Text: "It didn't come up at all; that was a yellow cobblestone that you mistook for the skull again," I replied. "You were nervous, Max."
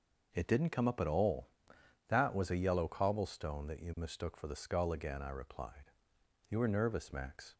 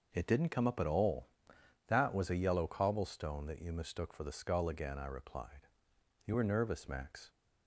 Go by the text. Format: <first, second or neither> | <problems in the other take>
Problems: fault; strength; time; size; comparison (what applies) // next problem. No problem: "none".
neither | none